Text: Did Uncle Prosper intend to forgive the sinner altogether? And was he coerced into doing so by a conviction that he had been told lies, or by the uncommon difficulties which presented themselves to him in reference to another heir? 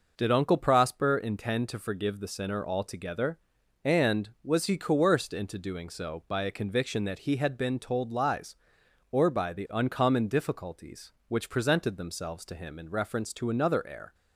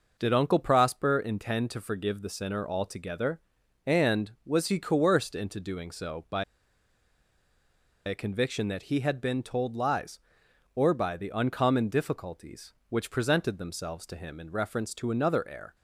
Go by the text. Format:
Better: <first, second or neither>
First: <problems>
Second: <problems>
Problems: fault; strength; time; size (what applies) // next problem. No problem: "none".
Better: first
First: none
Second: pauses between "by" and "a"; strong; at 6.4 s; 1.6 s long